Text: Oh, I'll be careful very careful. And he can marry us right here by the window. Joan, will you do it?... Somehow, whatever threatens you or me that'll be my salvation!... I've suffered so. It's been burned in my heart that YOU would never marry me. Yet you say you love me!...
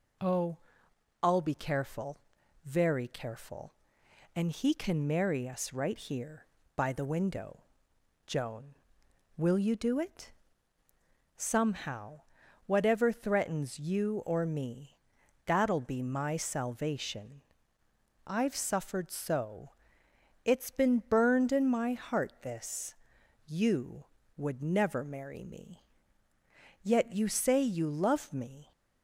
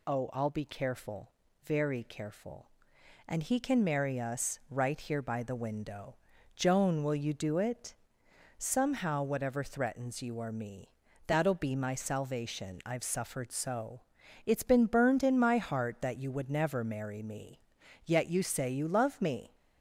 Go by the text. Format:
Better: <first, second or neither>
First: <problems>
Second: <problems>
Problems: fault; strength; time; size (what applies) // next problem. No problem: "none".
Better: second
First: pauses between "careful" and "very"; noticeable; at 2.1 s; 0.46 s long // pauses between "me" and "that'll"; noticeable; at 14.9 s; 0.52 s long // says "this" for "that"; at 22.4 s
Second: pauses between "careful" and "very"; slight; at 1.2 s; 0.34 s long // pauses between "me" and "that'll"; at 10.8 s; 0.40 s long